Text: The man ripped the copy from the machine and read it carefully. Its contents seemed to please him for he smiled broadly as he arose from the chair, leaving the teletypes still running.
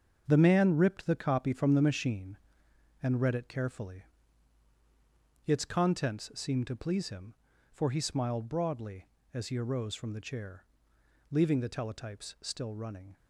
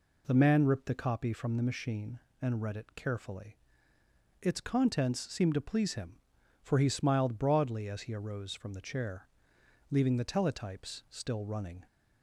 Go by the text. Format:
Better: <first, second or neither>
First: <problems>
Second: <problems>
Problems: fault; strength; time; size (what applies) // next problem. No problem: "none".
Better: second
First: gets quieter; strong; throughout; 9 dB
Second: none